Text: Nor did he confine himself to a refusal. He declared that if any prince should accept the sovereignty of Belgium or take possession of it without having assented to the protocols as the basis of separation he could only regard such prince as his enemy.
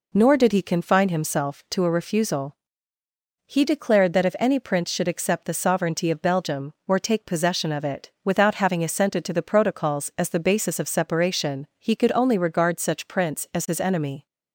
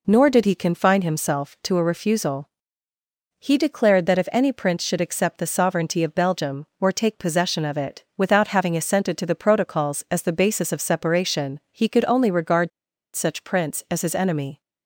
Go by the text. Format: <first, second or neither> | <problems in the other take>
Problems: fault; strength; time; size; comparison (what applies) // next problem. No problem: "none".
first | pauses between "regard" and "such"; noticeable; at 12.7 s; 0.46 s long